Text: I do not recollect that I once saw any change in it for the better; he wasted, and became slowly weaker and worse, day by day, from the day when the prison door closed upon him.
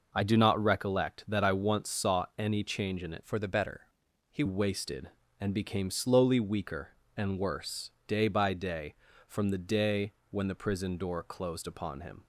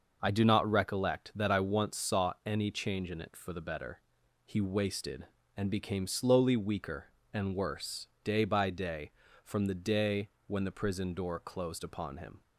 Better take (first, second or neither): second